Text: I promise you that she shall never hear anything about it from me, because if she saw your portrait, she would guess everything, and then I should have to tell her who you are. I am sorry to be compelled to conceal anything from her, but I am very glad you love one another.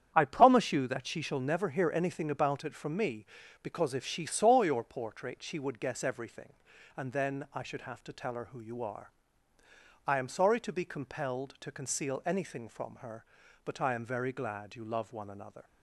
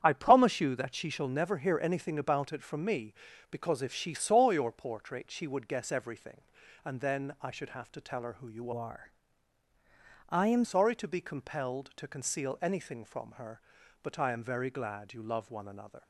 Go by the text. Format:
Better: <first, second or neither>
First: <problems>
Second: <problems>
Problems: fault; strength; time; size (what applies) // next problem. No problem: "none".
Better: first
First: starts louder than the rest; strong; until 1.1 s; 9 dB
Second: starts louder than the rest; strong; until 1.0 s; 9 dB // changes voice from "are" to "am"; from 8.7 to 10.6 s; 1.9 s long